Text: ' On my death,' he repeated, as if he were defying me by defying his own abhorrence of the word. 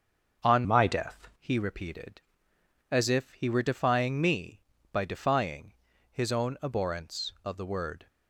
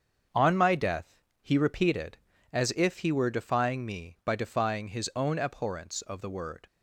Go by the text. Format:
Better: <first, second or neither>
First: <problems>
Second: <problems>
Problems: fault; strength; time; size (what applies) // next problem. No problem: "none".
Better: second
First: starts louder than the rest; until 1.5 s; 6.5 dB // changes voice from "my" to "death"; from 0.6 to 1.2 s; 0.6 s long // pauses between "defying" and "his"; slight; at 5.7 s; 0.36 s long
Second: starts louder than the rest; until 1.5 s; 7 dB